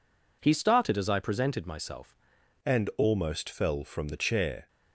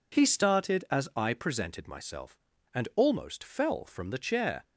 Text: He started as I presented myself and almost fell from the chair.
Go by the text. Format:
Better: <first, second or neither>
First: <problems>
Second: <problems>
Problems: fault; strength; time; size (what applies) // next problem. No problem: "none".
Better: second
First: changes voice at "and"; from 2.6 s on; 2.0 s long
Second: none